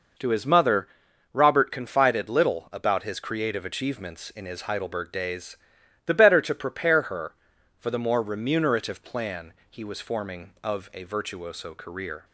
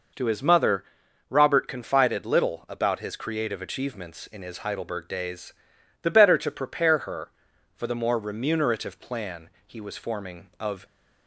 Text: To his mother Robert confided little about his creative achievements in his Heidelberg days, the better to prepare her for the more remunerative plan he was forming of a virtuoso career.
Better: first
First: pauses between "mother" and "Robert"; noticeable; at 0.8 s; 0.46 s long // pauses between "plan" and "he"; slight; at 9.5 s; 0.16 s long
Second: pauses between "mother" and "Robert"; noticeable; at 0.8 s; 0.46 s long // pauses between "plan" and "he"; slight; at 9.4 s; 0.16 s long // stops before "a virtuoso career"; at 10.8 s

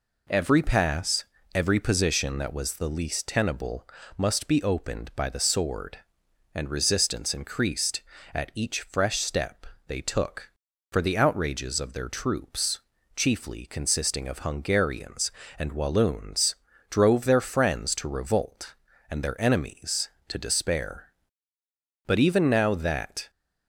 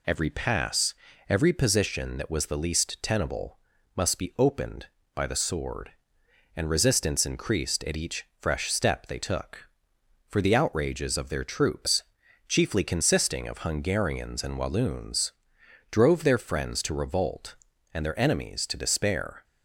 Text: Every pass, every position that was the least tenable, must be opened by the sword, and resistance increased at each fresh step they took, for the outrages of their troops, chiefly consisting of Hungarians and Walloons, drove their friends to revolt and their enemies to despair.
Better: second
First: pauses between "step" and "they"; slight; at 9.6 s; 0.20 s long // goes on to say "But even now that"; noticeable; from 22.0 s on; 1.2 s long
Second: none

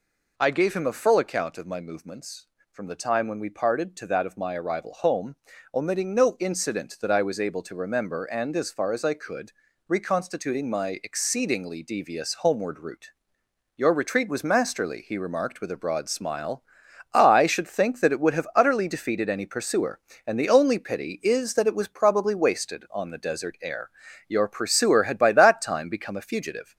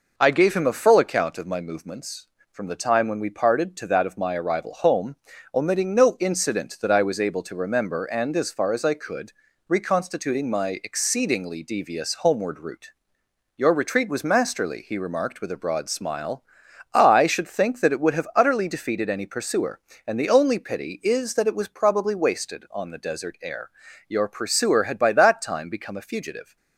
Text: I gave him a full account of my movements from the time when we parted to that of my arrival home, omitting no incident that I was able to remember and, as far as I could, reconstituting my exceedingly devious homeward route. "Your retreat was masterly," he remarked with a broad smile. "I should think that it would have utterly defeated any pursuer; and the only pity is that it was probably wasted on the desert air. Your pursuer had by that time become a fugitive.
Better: second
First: gets louder; throughout; 4 dB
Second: none

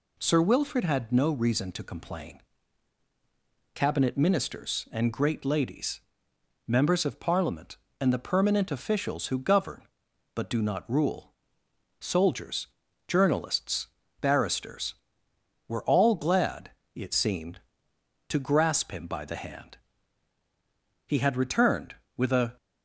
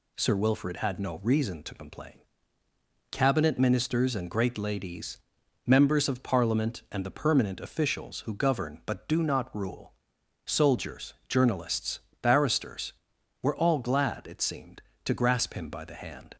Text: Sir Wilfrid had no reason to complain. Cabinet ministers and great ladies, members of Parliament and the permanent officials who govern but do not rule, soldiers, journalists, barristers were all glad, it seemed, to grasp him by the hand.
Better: second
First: goes on to say "He had returned with a"; from 21.0 s on; 1.4 s long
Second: none

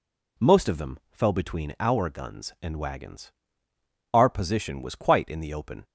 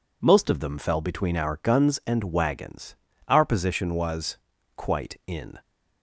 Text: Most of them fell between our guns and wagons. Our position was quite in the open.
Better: first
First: none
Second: pauses between "was" and "quite"; at 4.3 s; 0.40 s long // stops before "the open"; at 5.6 s

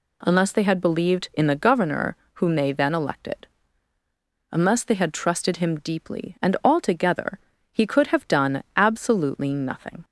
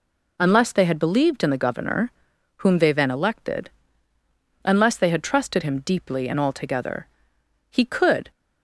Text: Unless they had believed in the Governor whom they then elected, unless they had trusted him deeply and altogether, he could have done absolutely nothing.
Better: first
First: pauses between "Governor" and "whom"; slight; at 2.1 s; 0.20 s long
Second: pauses between "Governor" and "whom"; noticeable; at 2.1 s; 0.46 s long // stops before "have done absolutely nothing"; at 8.3 s

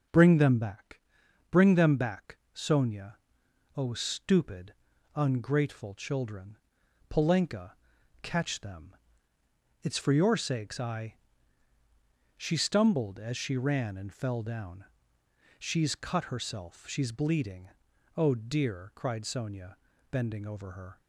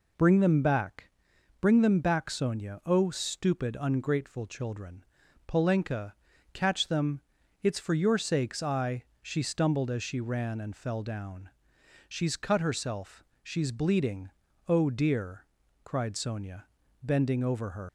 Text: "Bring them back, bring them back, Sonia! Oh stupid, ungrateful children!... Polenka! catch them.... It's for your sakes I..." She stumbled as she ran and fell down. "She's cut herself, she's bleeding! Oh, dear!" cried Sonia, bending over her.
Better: first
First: none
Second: leaves "her" unfinished; at 17.8 s; 95 ms

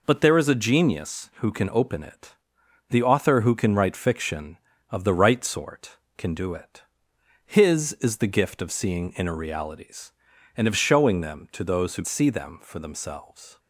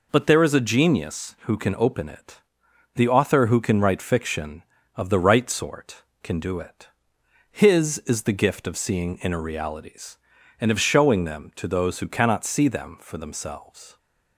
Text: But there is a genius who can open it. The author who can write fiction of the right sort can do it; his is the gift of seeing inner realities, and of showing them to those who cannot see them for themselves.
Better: second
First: skips "cannot"; at 12.0 s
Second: none

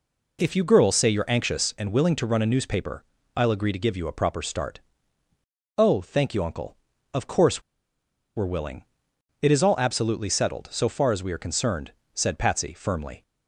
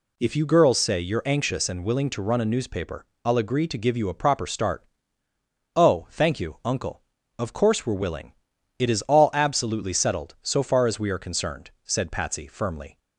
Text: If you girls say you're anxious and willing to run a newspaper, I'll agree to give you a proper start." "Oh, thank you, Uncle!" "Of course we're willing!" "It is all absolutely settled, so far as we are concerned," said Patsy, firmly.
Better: second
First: pauses between "course" and "we're"; noticeable; at 7.6 s; 0.74 s long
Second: none

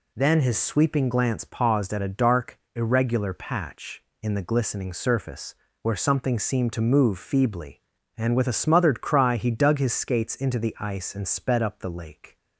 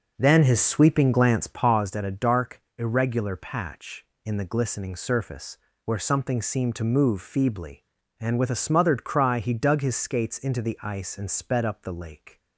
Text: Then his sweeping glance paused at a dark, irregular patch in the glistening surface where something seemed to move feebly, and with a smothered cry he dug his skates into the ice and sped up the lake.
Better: first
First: pauses between "surface" and "where"; slight; at 5.5 s; 0.28 s long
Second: starts louder than the rest; noticeable; until 1.9 s; 6 dB // pauses between "surface" and "where"; slight; at 5.5 s; 0.28 s long

